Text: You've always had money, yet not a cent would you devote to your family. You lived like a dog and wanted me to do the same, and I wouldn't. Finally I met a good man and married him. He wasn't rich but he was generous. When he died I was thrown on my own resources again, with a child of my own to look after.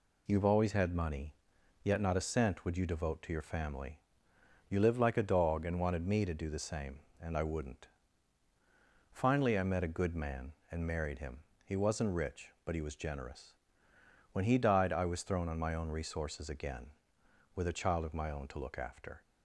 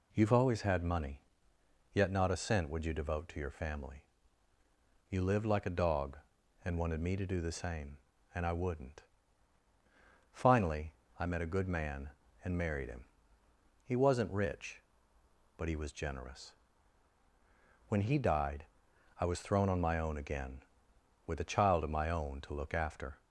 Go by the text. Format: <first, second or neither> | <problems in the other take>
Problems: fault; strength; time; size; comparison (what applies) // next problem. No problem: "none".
first | pauses between "Finally" and "I"; slight; at 10.9 s; 0.24 s long // pauses between "died" and "I"; noticeable; at 18.6 s; 0.56 s long // skips "resources"; at 20.1 s